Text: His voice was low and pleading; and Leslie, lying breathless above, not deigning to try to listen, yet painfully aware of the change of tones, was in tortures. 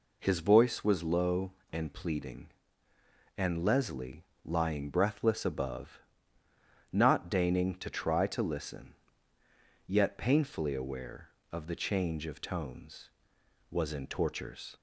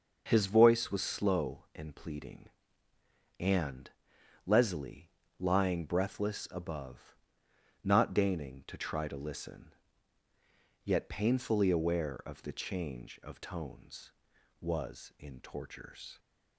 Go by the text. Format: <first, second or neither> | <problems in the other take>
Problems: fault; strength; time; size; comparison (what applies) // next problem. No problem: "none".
first | starts louder than the rest; noticeable; until 1.2 s; 6 dB // says "slow" for "low"; at 1.0 s // pauses between "and" and "Leslie"; noticeable; at 3.8 s; 0.56 s long